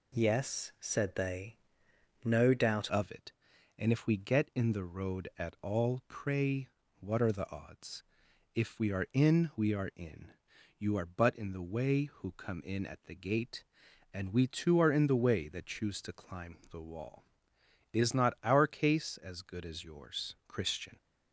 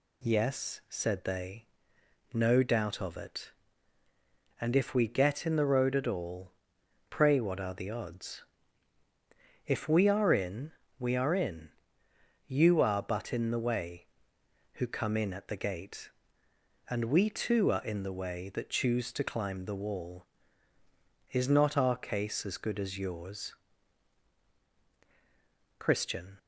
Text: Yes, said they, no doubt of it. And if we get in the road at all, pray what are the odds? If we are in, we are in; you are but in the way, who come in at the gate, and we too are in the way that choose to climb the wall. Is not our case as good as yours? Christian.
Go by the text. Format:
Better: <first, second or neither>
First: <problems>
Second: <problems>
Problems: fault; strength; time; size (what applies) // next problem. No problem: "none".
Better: second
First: changes voice at "of"; from 2.8 s on; 18.1 s long // pauses between "pray" and "what"; slight; at 6.6 s; 0.32 s long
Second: none